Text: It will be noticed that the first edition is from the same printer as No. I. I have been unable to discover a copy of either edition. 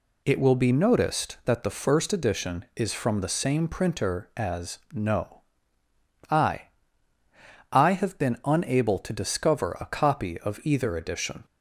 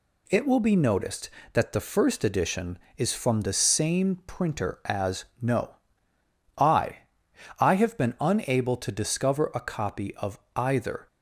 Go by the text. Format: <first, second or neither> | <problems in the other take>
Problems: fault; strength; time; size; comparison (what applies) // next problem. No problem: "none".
first | pauses between "as" and "No"; slight; at 5.2 s; 0.16 s long; slight in the first // pauses between "of" and "either"; slight; at 10.3 s; 0.16 s long // stops before "edition"; at 11.0 s